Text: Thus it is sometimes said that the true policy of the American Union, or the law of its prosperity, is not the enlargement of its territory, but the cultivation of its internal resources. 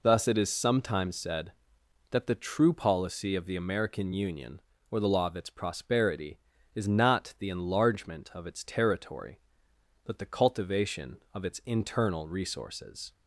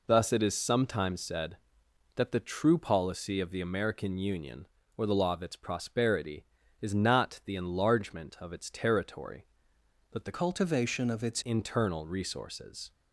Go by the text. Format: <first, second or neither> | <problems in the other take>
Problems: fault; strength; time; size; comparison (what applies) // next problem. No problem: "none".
first | changes voice from "cultivation" to "its"; from 10.3 to 11.4 s; 1.1 s long